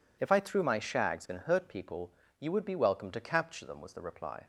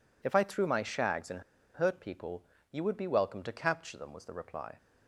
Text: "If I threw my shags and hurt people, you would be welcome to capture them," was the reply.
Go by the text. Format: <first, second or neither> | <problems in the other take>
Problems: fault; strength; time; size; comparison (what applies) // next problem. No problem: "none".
first | pauses between "and" and "hurt"; slight; at 1.4 s; 0.34 s long